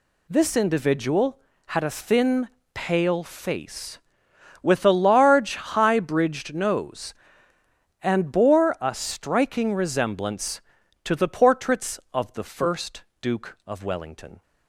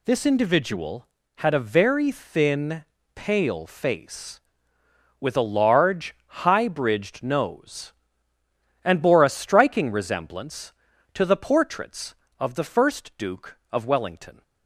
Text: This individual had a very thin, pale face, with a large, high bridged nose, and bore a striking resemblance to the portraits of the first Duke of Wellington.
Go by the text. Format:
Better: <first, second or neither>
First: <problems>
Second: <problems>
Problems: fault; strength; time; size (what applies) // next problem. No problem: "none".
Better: second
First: skips "very"; at 1.8 s // pauses between "first" and "Duke"; slight; at 13.0 s; 0.18 s long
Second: none